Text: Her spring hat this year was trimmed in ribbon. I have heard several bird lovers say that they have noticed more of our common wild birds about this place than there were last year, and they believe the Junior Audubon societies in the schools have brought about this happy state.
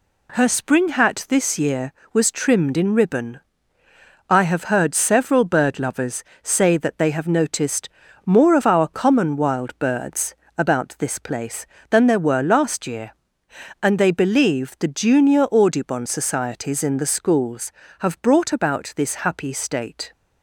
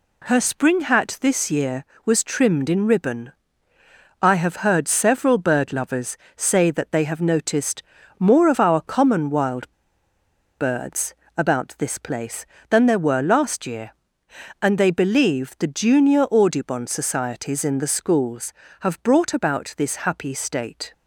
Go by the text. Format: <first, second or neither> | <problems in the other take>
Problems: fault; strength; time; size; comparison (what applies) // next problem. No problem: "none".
first | pauses between "lovers" and "say"; slight; at 6.1 s; 0.20 s long; slight in the first // pauses between "noticed" and "more"; at 7.8 s; 0.38 s long; also in the first // pauses between "wild" and "birds"; noticeable; at 9.6 s; 0.93 s long // pauses between "birds" and "about"; slight; at 11.1 s; 0.20 s long; slight in the first